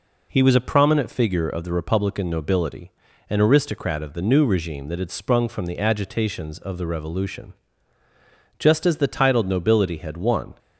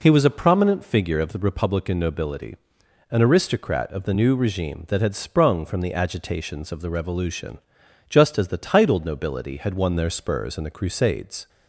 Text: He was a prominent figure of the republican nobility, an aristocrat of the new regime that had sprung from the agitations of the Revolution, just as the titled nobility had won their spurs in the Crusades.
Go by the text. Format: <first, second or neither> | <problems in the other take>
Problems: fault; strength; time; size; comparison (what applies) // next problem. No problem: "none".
second | stops before "their spurs in the Crusades"; at 10.5 s